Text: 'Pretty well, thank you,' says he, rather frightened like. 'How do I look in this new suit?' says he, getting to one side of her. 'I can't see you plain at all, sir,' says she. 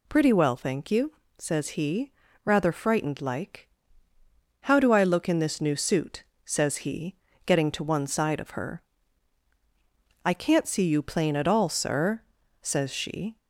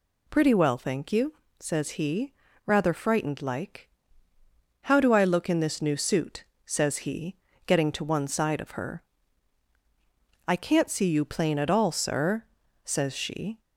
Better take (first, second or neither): neither